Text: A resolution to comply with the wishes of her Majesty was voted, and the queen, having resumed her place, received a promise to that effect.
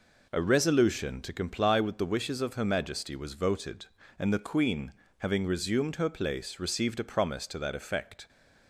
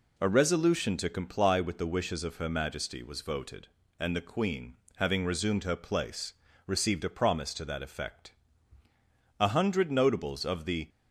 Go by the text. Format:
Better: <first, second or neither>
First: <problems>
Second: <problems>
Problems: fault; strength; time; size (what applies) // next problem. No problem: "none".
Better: first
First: none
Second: goes on to say "A hundred notables of the"; from 9.3 s on; 1.5 s long